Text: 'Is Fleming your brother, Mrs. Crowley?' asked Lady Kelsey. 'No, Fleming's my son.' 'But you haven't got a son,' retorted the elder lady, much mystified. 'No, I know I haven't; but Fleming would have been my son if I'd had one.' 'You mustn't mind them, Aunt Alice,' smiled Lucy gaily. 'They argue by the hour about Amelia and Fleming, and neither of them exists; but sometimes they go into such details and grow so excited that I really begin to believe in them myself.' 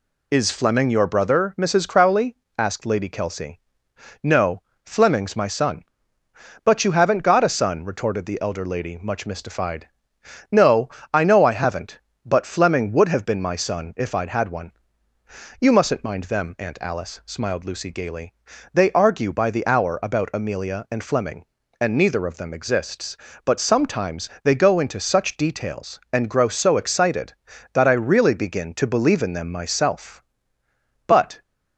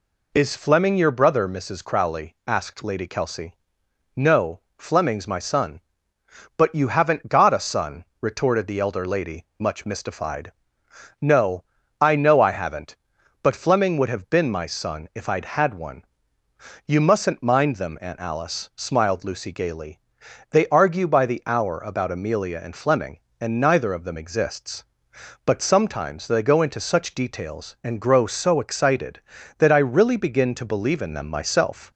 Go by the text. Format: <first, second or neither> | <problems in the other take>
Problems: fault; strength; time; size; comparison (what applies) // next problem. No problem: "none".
second | goes on to say "But"; slight; from 31.0 s on; 0.36 s long